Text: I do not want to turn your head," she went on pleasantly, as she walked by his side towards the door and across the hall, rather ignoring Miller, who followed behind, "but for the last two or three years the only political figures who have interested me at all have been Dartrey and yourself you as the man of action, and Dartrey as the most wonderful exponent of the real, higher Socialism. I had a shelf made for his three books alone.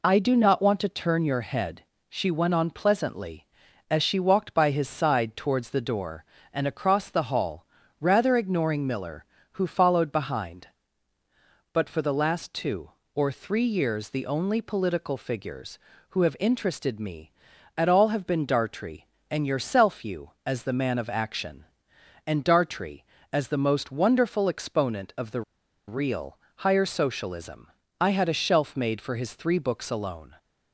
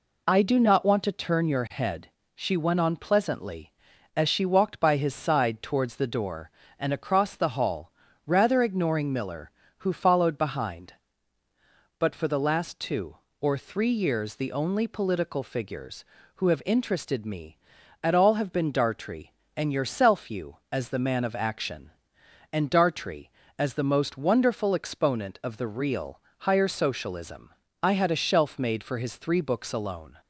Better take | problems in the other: second | pauses between "the" and "real"; noticeable; at 25.4 s; 0.46 s long

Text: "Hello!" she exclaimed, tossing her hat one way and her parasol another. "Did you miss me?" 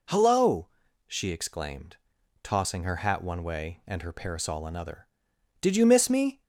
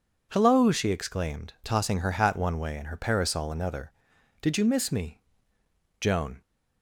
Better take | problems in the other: first | goes on to say "Joan"; slight; from 6.0 s on; 0.40 s long

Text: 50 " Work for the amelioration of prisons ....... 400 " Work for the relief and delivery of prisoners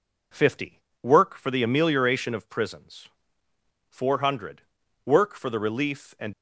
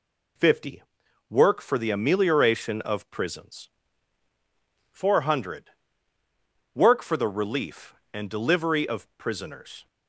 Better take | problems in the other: second | stops before "delivery of prisoners"; at 6.3 s

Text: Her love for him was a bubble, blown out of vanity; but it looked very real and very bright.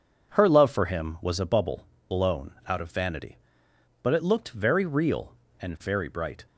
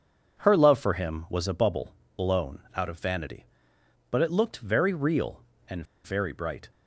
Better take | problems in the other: first | pauses between "blown" and "out"; slight; at 2.5 s; 0.16 s long; slight in the first // pauses between "and" and "very"; slight; at 5.8 s; 0.20 s long

